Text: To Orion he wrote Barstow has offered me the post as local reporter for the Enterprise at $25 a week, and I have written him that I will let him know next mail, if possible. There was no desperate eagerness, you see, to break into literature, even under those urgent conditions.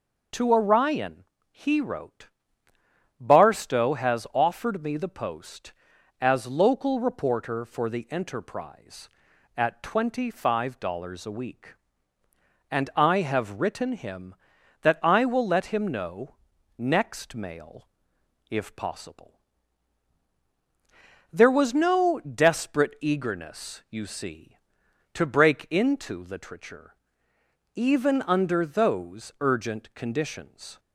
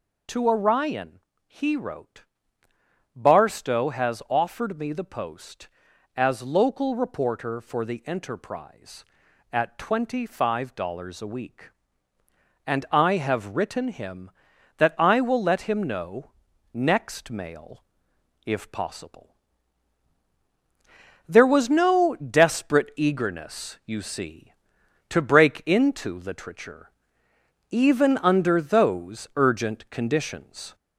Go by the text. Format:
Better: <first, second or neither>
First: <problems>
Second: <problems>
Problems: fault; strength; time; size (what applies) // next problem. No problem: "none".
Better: first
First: pauses between "Orion" and "he"; slight; at 1.2 s; 0.28 s long // pauses between "wrote" and "Barstow"; noticeable; at 2.2 s; 0.92 s long // pauses between "know" and "next"; at 16.3 s; 0.42 s long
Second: gets louder; slight; throughout; 2.5 dB // pauses between "Orion" and "he"; slight; at 1.1 s; 0.28 s long // pauses between "wrote" and "Barstow"; noticeable; at 2.2 s; 0.92 s long // pauses between "know" and "next"; at 16.3 s; 0.42 s long